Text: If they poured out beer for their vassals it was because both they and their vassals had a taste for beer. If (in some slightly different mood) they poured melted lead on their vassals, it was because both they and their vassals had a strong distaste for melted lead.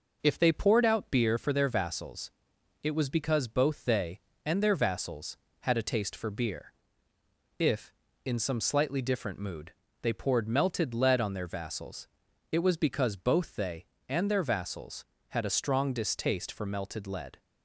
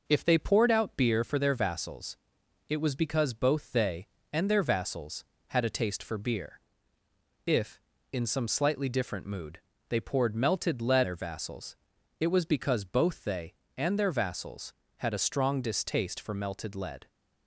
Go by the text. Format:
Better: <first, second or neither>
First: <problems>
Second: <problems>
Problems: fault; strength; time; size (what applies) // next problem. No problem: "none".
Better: first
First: pauses between "vassals" and "it"; noticeable; at 2.2 s; 0.52 s long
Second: pauses between "vassals" and "it"; noticeable; at 2.1 s; 0.52 s long // skips "on"; at 11.0 s